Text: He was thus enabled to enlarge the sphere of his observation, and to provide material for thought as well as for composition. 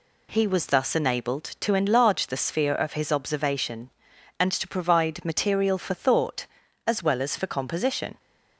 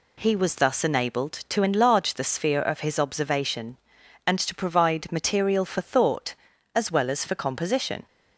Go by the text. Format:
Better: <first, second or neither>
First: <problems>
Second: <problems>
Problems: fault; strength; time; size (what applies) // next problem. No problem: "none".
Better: neither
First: none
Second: none